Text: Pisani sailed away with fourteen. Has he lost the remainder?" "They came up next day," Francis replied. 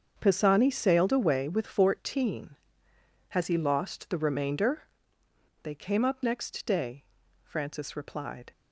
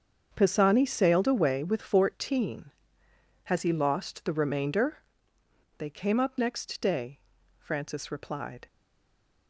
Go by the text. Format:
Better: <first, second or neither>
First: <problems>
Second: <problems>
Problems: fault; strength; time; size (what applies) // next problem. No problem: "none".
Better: first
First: starts louder than the rest; strong; until 1.2 s; 7 dB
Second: starts louder than the rest; strong; until 1.3 s; 7 dB // stays silent after the last word; slight; from 8.6 s on; 0.8 s long